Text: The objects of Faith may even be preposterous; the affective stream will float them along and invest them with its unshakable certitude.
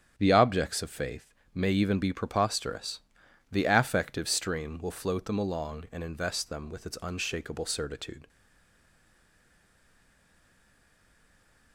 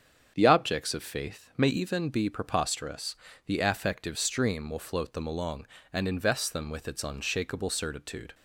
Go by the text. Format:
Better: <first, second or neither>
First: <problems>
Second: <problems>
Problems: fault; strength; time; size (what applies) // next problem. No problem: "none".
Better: second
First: starts louder than the rest; strong; until 1.1 s; 8.5 dB // pauses between "Faith" and "may"; slight; at 1.3 s; 0.18 s long // stays silent after the last word; strong; from 8.2 s on; 3.5 s long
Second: starts louder than the rest; strong; until 1.3 s; 7.5 dB